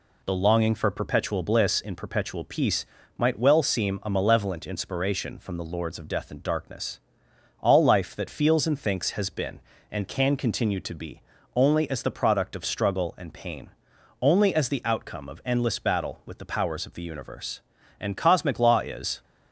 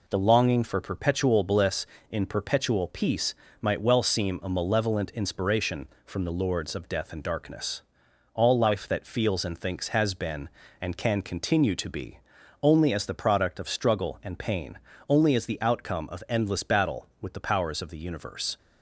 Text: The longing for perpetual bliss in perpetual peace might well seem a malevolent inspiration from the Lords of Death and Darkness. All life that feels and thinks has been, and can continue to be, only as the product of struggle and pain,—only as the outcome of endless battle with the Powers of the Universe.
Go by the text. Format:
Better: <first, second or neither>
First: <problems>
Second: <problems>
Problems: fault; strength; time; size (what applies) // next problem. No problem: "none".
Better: second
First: pauses between "peace" and "might"; slight; at 2.8 s; 0.32 s long // goes on to say "And cosmic law is"; noticeable; from 17.9 s on; 1.2 s long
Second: pauses between "peace" and "might"; slight; at 3.3 s; 0.26 s long